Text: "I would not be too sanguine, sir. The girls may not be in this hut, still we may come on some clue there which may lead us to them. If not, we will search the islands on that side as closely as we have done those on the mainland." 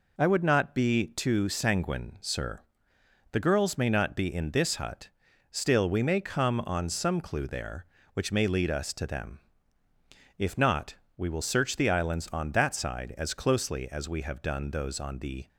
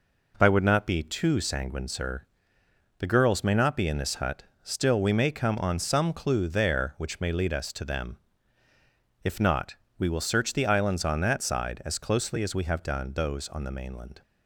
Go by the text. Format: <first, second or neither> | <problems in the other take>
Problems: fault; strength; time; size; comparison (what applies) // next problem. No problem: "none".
second | stops before "mainland"; at 15.4 s